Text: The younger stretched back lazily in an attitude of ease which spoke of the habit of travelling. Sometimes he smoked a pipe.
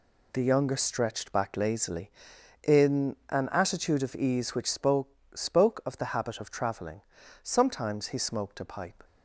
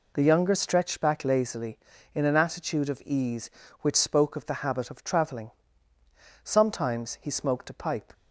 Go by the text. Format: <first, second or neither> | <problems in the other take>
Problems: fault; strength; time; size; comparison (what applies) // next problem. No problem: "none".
second | says "spoke" twice; at 5.3 s